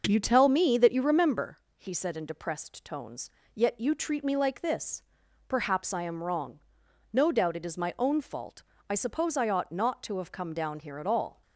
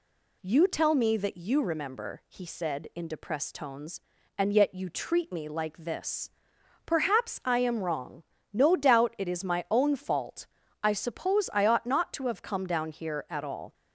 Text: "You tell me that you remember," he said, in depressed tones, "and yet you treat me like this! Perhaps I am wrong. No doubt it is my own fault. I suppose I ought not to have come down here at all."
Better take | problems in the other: second | starts louder than the rest; noticeable; until 1.0 s; 6 dB // skips "and"; at 3.4 s

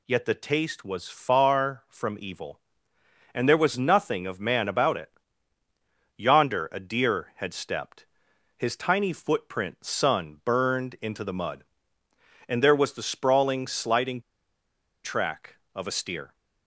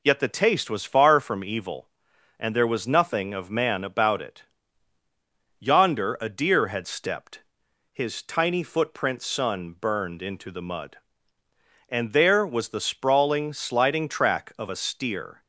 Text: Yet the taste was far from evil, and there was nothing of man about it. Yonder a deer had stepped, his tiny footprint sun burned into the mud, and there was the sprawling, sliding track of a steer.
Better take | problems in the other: second | pauses between "sliding" and "track"; noticeable; at 14.1 s; 0.84 s long

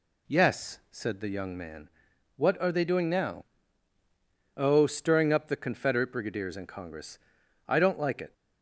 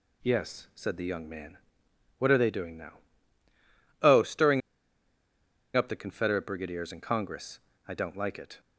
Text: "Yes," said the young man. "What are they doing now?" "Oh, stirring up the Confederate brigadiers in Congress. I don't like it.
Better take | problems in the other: first | pauses between "stirring" and "up"; at 4.6 s; 1.1 s long

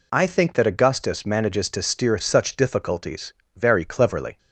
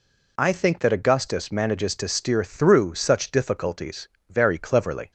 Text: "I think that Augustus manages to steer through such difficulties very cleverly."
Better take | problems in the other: second | skips "through"; at 2.1 s // pauses between "difficulties" and "very"; slight; at 3.3 s; 0.22 s long; slight in the second

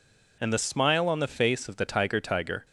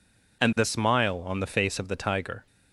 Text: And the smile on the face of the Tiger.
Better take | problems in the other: second | says "Tiger" twice; at 2.1 s

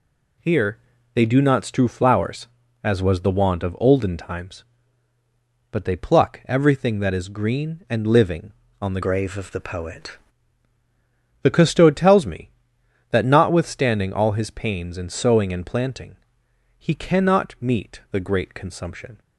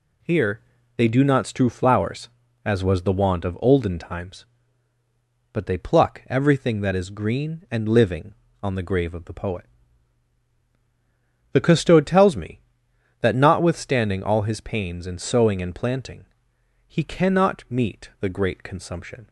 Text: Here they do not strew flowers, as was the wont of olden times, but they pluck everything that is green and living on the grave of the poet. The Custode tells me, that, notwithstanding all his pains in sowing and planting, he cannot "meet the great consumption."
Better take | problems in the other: second | pauses between "Here" and "they"; slight; at 0.7 s; 0.36 s long; slight in the second // changes voice from "grave" to "poet"; from 9.0 to 10.1 s; 1.1 s long

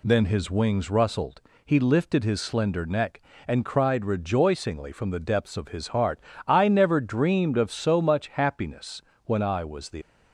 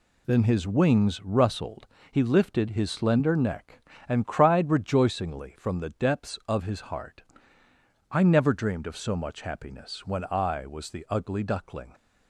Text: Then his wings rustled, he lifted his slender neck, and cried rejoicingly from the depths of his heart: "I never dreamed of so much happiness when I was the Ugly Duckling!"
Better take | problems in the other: second | pauses between "happiness" and "when"; slight; at 9.0 s; 0.24 s long // stops before "Ugly Duckling"; at 10.0 s

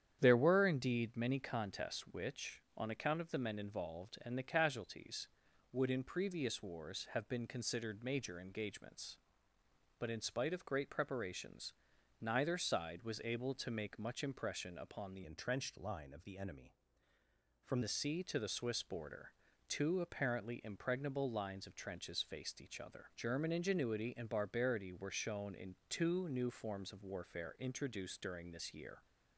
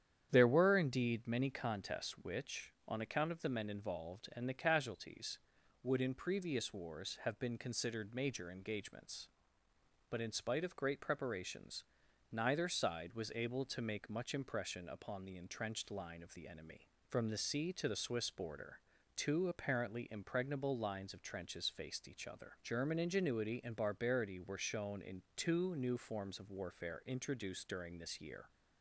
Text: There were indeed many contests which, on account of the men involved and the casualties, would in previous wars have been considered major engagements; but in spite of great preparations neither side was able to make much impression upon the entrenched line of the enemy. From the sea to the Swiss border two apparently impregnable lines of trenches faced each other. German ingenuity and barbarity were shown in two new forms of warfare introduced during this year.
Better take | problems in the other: second | starts louder than the rest; strong; until 1.2 s; 9 dB; strong in the second // pauses between "preparations" and "neither"; noticeable; at 11.7 s; 0.48 s long; noticeable in the second // changes voice from "entrenched" to "From"; from 15.2 to 17.7 s; 2.5 s long // pauses between "border" and "two"; slight; at 19.3 s; 0.34 s long; slight in the second

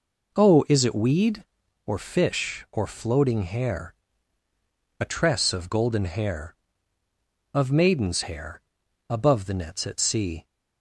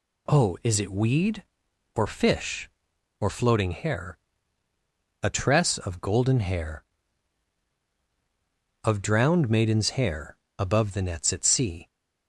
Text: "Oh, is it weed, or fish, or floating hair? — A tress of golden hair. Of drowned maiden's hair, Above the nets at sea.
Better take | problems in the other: second | skips "drowned"; at 7.7 s

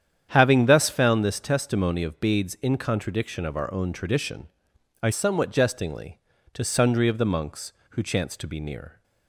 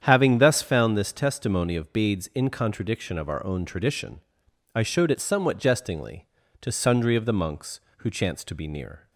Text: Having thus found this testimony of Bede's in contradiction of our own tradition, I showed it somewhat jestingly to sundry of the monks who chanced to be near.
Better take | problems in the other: second | starts louder than the rest; strong; until 1.3 s; 9 dB; strong in the second // skips "showed it"; at 5.1 s

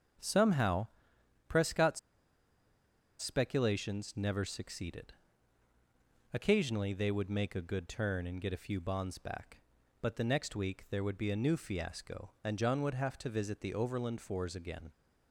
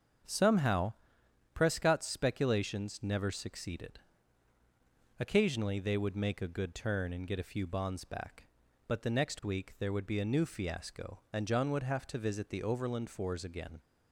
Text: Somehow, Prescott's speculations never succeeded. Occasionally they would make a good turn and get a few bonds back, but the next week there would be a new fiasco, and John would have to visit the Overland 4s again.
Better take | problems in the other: second | starts louder than the rest; until 1.8 s; 7 dB; also in the second // pauses between "Prescott's" and "speculations"; at 1.9 s; 1.2 s long

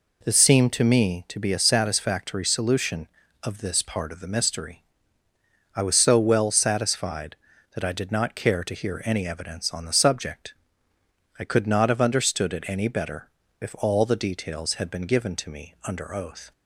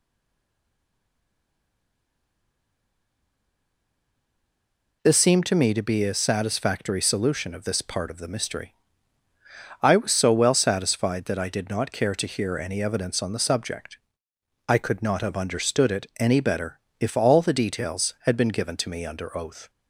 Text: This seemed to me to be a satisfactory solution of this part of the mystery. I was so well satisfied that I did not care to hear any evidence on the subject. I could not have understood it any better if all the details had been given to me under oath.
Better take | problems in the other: first | stays silent before the first word; strong; until 5.0 s; 5.0 s long // pauses between "better" and "if"; slight; at 16.7 s; 0.20 s long; slight in the first

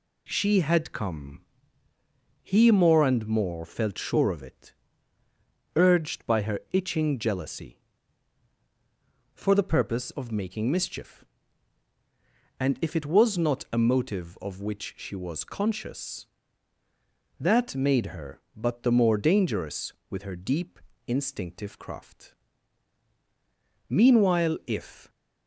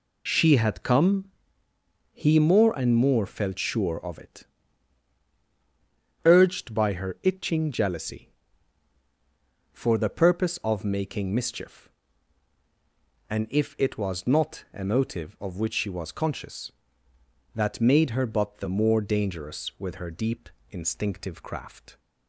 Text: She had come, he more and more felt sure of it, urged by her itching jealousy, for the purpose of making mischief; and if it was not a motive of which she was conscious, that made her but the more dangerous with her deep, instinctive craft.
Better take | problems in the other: second | goes on to say "Meanwhile if"; noticeable; from 23.8 s on; 1.2 s long

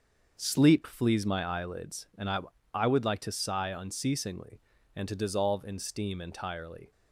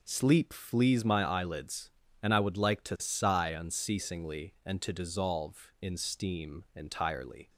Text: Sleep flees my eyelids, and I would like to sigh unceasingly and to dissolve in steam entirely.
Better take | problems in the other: second | starts louder than the rest; until 1.4 s; 6.5 dB // says "I" twice; at 2.7 s

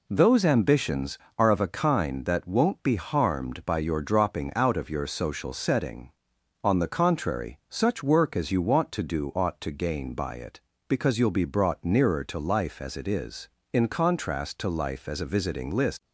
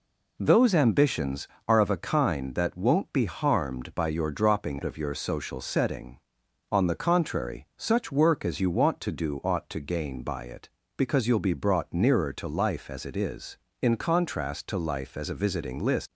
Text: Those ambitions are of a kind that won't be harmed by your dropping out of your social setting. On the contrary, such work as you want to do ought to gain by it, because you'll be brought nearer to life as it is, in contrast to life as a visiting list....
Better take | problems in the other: first | skips "out"; at 4.8 s

